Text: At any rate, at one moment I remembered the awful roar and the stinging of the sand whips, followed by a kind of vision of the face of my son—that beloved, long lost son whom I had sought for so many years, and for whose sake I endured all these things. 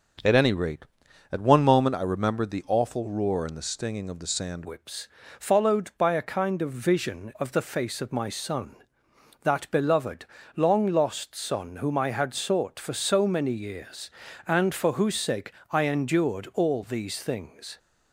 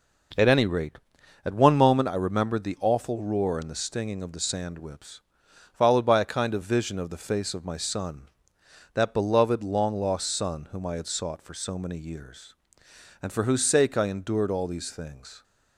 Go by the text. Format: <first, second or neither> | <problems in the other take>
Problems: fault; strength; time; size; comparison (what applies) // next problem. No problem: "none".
second | starts louder than the rest; until 1.7 s; 6.5 dB // changes voice at "whips"; from 4.6 s on; 13.1 s long // pauses between "sake" and "I"; slight; at 15.5 s; 0.18 s long